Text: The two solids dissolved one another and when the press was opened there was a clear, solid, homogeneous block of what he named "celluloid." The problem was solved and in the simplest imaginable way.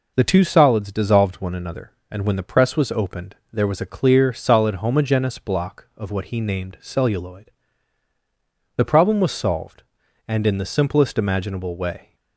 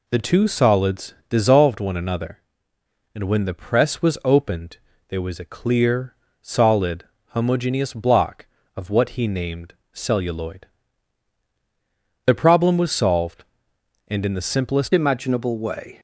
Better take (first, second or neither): first